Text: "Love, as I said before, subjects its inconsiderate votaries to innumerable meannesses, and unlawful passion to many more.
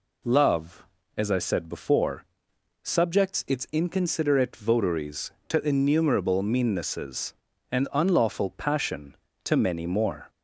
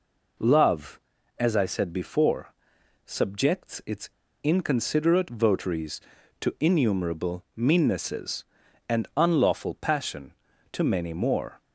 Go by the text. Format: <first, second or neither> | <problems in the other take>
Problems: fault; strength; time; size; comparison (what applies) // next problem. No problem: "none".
first | pauses between "its" and "inconsiderate"; slight; at 4.0 s; 0.34 s long